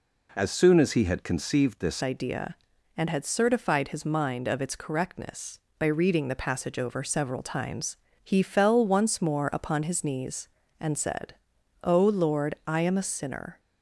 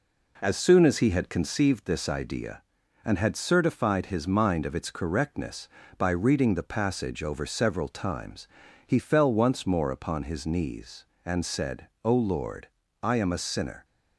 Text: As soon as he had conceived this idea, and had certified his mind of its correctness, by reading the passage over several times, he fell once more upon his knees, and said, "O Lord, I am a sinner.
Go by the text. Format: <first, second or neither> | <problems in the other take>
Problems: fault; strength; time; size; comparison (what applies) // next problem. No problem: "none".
second | changes voice at "idea"; from 2.0 s on; 11.5 s long